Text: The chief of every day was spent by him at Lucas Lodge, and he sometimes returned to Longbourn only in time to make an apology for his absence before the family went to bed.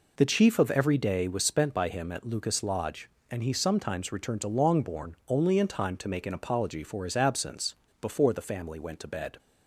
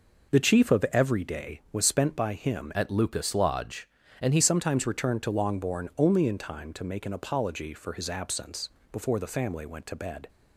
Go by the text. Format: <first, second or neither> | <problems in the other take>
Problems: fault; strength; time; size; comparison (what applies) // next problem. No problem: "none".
first | changes voice from "at" to "he"; from 2.7 to 4.3 s; 1.6 s long // pauses between "absence" and "before"; slight; at 8.6 s; 0.24 s long; slight in the first